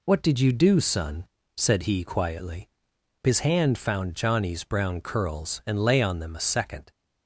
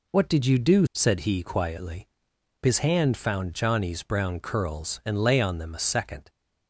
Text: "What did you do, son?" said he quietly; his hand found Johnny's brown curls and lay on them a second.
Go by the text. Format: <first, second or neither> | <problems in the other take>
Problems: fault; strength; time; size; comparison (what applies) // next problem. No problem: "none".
first | skips "son"; at 0.8 s